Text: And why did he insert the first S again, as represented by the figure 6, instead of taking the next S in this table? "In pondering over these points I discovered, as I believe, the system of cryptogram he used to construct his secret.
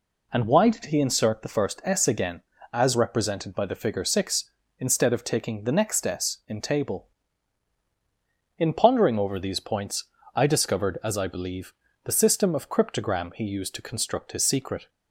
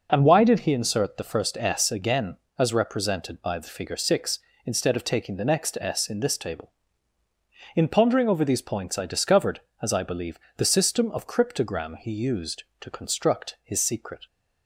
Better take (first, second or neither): second